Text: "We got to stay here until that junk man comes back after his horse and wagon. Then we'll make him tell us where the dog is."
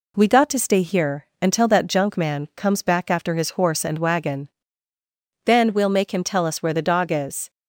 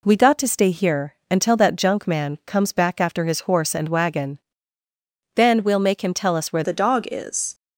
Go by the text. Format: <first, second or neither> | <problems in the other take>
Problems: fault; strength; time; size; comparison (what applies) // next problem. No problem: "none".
first | pauses between "here" and "until"; slight; at 1.1 s; 0.16 s long; slight in the first // changes voice at "the"; from 6.6 s on; 0.9 s long